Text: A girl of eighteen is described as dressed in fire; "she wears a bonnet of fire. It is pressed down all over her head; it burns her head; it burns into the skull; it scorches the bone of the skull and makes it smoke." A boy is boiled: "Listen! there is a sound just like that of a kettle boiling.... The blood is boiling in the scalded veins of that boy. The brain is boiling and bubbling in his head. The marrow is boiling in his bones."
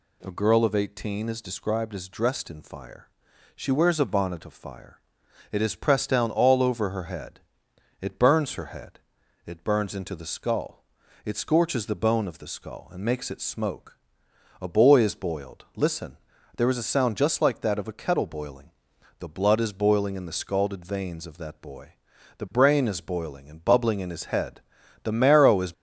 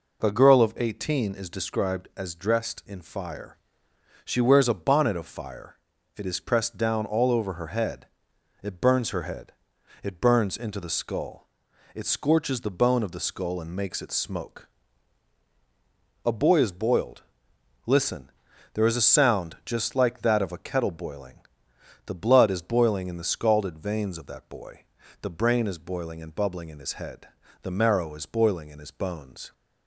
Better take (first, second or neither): second